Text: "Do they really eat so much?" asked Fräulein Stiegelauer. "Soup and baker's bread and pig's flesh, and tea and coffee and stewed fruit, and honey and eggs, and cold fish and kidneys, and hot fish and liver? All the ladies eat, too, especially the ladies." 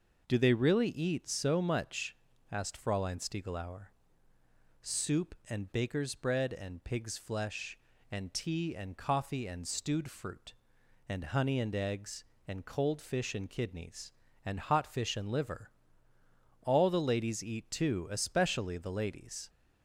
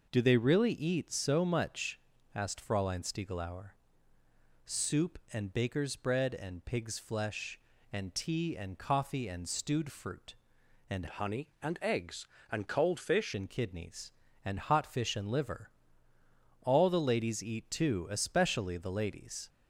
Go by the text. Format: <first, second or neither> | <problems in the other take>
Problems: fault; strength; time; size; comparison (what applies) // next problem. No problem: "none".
first | changes voice from "honey" to "fish"; from 11.0 to 13.3 s; 2.3 s long